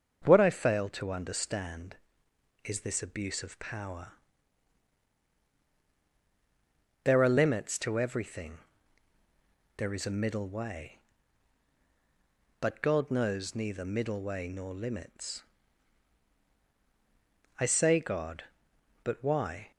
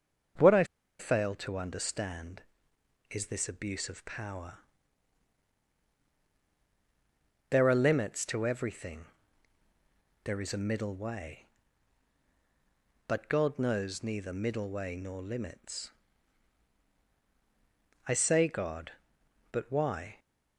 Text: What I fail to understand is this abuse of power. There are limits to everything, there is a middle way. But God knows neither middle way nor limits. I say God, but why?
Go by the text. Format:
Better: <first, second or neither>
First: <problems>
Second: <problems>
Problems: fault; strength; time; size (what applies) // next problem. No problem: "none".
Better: first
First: starts louder than the rest; until 1.2 s; 7 dB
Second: starts louder than the rest; until 1.7 s; 7 dB // pauses between "I" and "fail"; slight; at 0.6 s; 0.34 s long